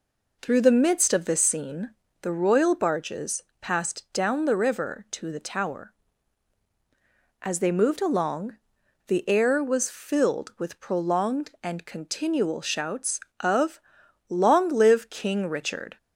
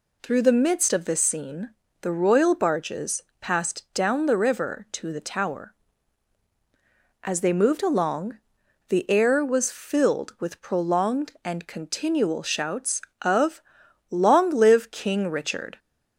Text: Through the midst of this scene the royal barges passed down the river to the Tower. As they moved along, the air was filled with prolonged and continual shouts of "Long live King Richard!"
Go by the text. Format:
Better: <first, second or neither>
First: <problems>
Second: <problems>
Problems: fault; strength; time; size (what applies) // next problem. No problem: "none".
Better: second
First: starts louder than the rest; noticeable; until 2.3 s; 4.5 dB // pauses between "scene" and "the"; slight; at 1.9 s; 0.30 s long // pauses between "barges" and "passed"; slight; at 3.4 s; 0.18 s long // pauses between "of" and "Long"; noticeable; at 13.7 s; 0.50 s long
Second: pauses between "scene" and "the"; slight; at 1.7 s; 0.30 s long // pauses between "barges" and "passed"; slight; at 3.2 s; 0.18 s long // pauses between "of" and "Long"; noticeable; at 13.6 s; 0.50 s long